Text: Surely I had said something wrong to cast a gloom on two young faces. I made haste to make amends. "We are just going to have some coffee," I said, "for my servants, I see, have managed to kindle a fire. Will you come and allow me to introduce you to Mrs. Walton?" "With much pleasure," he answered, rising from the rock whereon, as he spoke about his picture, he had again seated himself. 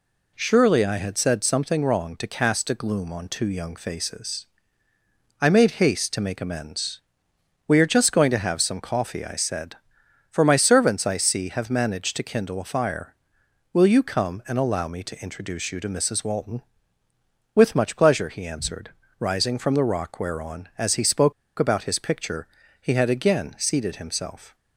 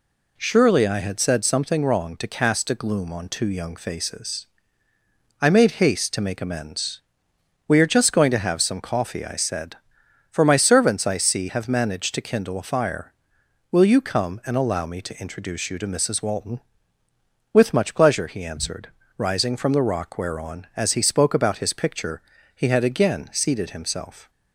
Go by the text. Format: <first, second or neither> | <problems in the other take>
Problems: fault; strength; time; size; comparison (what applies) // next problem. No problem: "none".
second | pauses between "spoke" and "about"; slight; at 21.3 s; 0.26 s long